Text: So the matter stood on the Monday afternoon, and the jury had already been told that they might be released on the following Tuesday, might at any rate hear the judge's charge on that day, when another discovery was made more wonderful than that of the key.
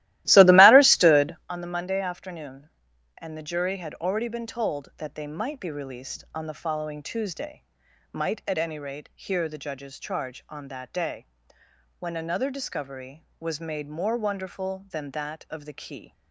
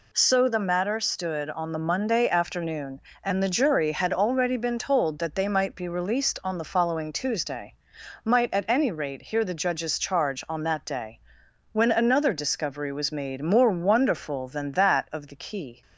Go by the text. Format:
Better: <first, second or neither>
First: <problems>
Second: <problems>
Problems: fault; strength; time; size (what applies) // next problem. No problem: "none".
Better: second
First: starts louder than the rest; strong; until 1.5 s; 16 dB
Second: none